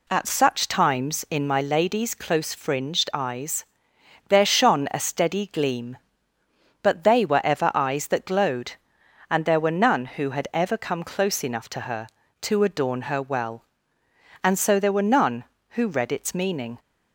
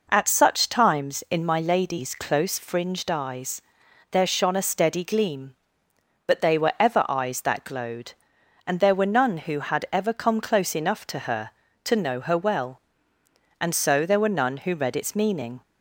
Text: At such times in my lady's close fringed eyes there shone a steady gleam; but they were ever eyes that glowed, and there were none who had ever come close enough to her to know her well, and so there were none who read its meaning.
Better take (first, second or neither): second